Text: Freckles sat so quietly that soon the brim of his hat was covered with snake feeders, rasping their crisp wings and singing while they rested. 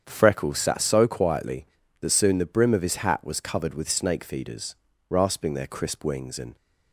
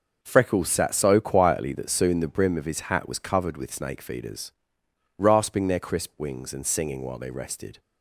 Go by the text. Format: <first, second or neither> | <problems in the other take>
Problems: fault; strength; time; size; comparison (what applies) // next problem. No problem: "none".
second | starts louder than the rest; strong; until 1.0 s; 8 dB; noticeable in the second // stops before "singing while they rested"; at 6.5 s